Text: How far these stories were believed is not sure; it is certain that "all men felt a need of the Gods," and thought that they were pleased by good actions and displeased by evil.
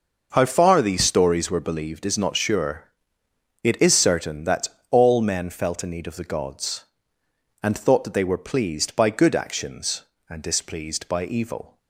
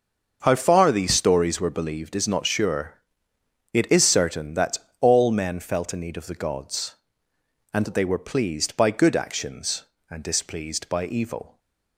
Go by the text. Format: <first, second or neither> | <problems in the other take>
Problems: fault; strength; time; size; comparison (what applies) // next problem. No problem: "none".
first | starts louder than the rest; until 1.4 s; 6.5 dB // pauses between "that" and "all"; slight; at 4.7 s; 0.22 s long; slight in the first // skips "thought"; at 7.8 s